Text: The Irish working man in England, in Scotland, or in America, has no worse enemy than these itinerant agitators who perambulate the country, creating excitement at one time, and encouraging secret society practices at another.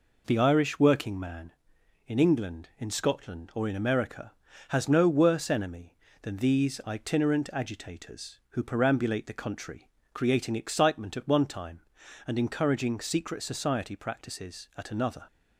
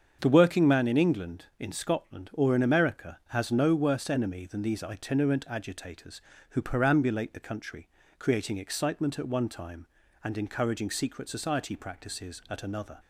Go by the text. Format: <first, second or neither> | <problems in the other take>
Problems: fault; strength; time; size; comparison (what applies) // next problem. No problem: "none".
first | starts louder than the rest; strong; until 1.2 s; 7 dB // skips "Irish"; at 0.3 s